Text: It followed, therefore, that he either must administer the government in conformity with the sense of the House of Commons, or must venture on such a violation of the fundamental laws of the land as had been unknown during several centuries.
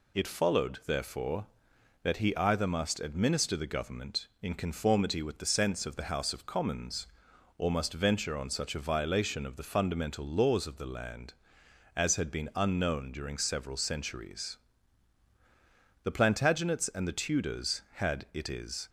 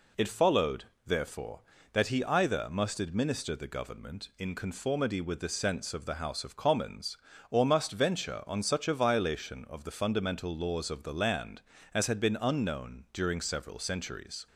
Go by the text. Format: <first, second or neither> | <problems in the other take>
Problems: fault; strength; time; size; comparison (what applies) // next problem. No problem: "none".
second | goes on to say "The Plantagenets and the Tudors had it is"; strong; from 16.0 s on; 2.8 s long